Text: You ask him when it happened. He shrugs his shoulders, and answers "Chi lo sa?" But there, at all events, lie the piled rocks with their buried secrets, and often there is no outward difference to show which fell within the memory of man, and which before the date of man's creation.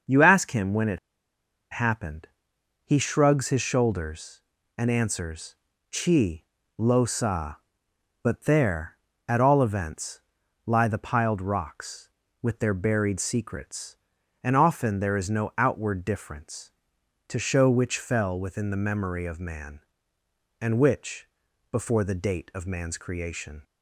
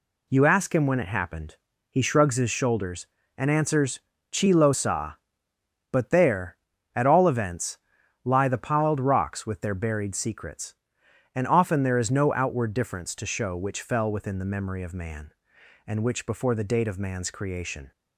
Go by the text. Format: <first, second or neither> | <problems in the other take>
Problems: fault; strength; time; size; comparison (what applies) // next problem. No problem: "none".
second | starts louder than the rest; until 1.8 s; 6 dB // pauses between "it" and "happened"; noticeable; at 0.9 s; 0.72 s long // pauses between "answers" and "Chi"; slight; at 5.5 s; 0.36 s long; slight in the second // pauses between "Chi" and "lo"; slight; at 6.4 s; 0.34 s long // pauses between "which" and "before"; at 21.2 s; 0.44 s long